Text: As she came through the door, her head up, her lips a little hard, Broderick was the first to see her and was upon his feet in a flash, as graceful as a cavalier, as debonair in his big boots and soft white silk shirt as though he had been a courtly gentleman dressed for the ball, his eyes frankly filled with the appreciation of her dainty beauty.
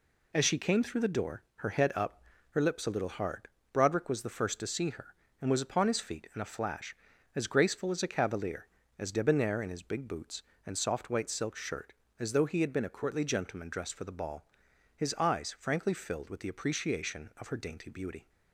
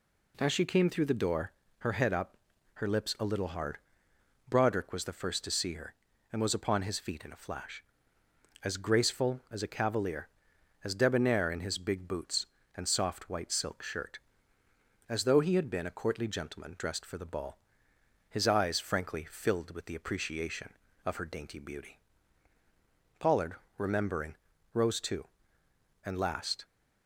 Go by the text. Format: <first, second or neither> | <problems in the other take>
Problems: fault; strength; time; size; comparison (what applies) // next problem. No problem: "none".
first | goes on to say "Pollard remembering rose too and last"; strong; from 23.1 s on; 3.4 s long